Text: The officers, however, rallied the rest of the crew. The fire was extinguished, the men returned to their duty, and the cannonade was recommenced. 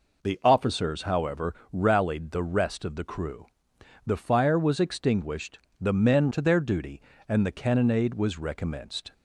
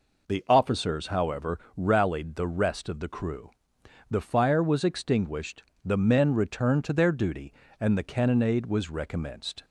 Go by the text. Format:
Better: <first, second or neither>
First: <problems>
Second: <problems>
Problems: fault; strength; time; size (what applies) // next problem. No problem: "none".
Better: second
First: skips "returned"; at 6.3 s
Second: none